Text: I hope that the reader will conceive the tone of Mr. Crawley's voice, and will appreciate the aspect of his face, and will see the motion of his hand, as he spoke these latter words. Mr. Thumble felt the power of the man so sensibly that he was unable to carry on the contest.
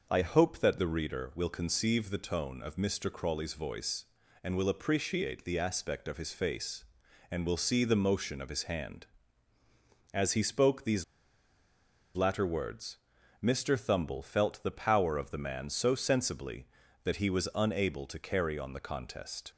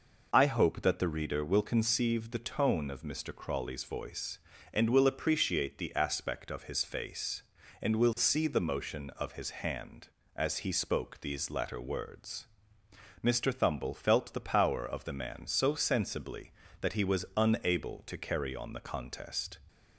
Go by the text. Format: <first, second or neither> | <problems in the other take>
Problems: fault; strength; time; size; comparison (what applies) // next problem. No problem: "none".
second | pauses between "these" and "latter"; at 11.0 s; 1.1 s long